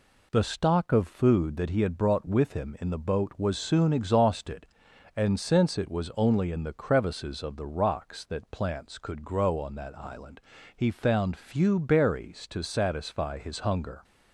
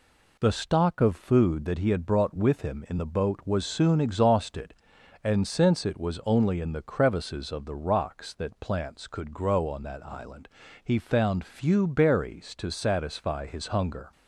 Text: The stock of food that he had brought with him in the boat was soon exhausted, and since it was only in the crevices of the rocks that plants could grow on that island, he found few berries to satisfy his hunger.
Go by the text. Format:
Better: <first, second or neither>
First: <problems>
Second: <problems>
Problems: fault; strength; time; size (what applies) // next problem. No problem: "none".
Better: neither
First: none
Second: none